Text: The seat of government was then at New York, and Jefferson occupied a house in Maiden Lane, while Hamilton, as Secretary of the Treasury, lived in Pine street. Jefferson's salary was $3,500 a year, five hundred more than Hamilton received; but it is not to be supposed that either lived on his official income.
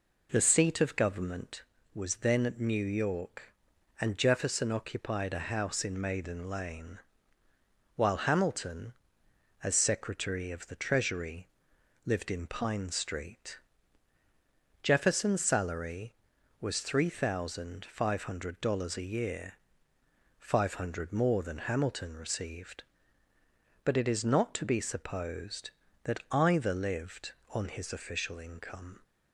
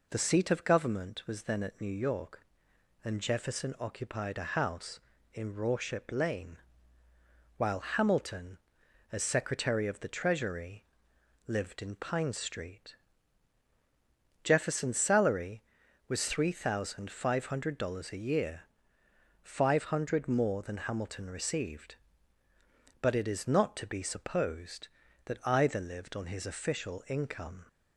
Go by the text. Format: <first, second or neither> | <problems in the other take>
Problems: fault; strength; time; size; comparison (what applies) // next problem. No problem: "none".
first | says "Rorship" for "Maiden"; at 5.5 s